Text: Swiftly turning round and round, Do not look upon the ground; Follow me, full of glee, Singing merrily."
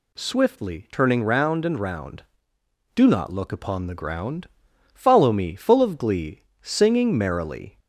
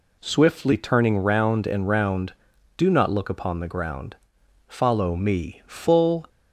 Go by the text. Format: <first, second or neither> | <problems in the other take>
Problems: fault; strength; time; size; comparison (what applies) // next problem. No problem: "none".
first | stops before "of glee Singing merrily"; at 6.2 s